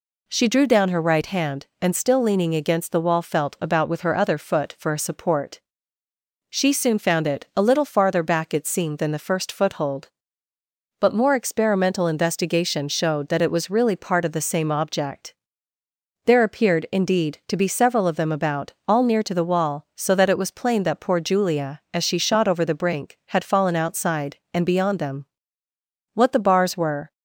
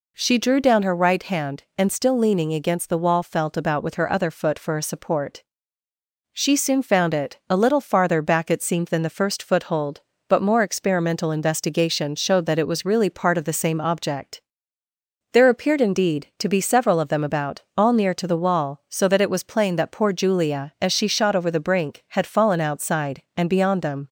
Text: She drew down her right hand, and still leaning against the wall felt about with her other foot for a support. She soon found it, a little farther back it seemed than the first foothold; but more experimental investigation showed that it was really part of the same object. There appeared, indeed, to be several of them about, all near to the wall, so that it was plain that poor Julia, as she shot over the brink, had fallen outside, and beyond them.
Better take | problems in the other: second | goes on to say "What the bars were"; noticeable; from 26.1 s on; 0.98 s long

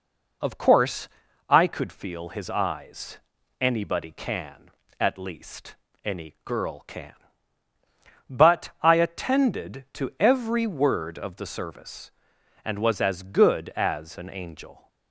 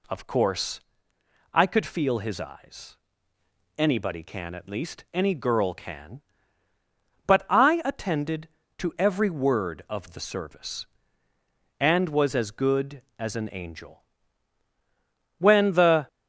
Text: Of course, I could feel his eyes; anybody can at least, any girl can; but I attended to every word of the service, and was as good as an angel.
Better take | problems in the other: first | goes on to say "When the"; noticeable; from 15.3 s on; 0.68 s long

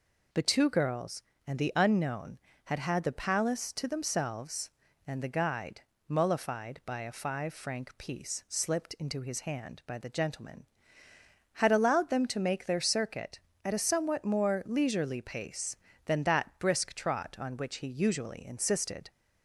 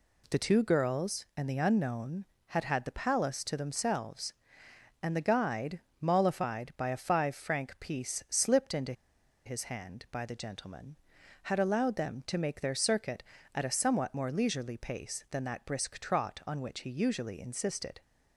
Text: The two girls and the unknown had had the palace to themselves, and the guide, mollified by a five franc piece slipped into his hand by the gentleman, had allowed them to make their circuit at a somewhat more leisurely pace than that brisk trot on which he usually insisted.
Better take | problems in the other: first | pauses between "into" and "his"; noticeable; at 8.9 s; 0.52 s long

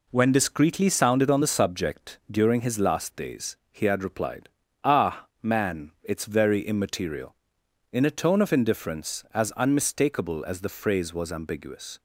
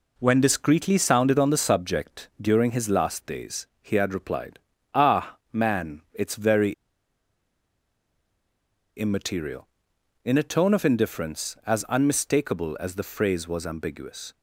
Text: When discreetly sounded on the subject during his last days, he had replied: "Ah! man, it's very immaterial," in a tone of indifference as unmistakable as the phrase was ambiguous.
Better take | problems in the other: first | pauses between "very" and "immaterial"; strong; at 6.7 s; 2.2 s long

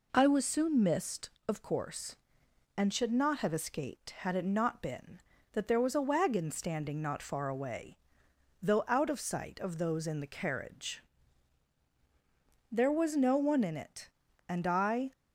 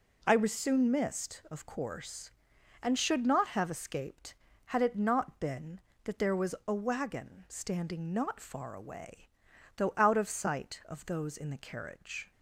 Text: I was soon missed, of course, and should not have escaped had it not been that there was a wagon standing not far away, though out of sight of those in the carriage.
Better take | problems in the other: second | goes on to say "There was no one in it and I"; strong; from 12.7 s on; 2.4 s long

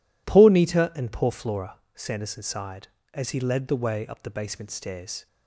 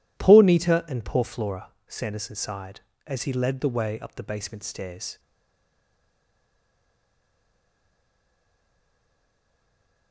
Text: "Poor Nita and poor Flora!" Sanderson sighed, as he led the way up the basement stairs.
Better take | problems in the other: first | stays silent after the last word; strong; from 5.1 s on; 5.0 s long

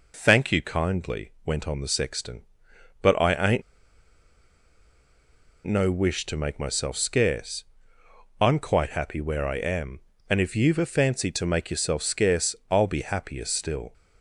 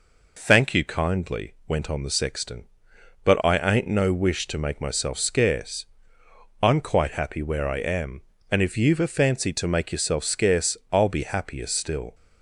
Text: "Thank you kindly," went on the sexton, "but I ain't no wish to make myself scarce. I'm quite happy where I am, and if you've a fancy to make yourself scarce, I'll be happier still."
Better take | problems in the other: second | pauses between "ain't" and "no"; strong; at 3.6 s; 2.0 s long

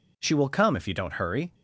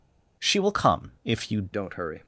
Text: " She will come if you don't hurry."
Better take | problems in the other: first | changes voice at "don't"; from 1.7 s on; 0.5 s long

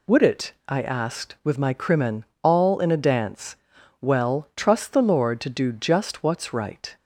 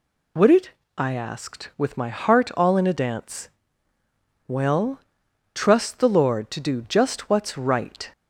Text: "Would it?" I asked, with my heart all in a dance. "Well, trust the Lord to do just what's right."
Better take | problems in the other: second | says "crimen" for "heart"; at 1.7 s

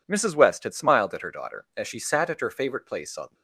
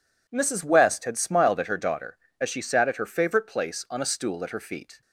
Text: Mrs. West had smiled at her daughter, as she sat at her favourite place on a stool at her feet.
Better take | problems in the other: second | stops before "a stool at her feet"; at 3.3 s

